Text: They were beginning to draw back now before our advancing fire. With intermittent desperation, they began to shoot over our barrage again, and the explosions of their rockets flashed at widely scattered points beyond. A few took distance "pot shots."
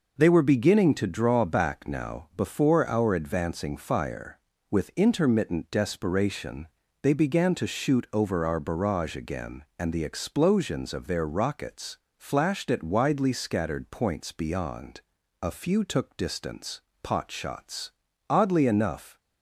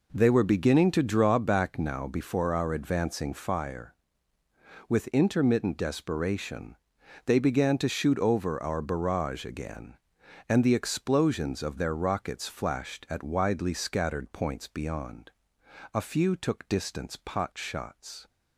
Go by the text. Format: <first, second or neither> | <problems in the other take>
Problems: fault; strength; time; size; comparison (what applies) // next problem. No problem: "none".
second | pauses between "rockets" and "flashed"; slight; at 11.9 s; 0.20 s long // pauses between "distance" and "pot"; slight; at 16.8 s; 0.22 s long // goes on to say "Oddly enough"; noticeable; from 18.3 s on; 0.88 s long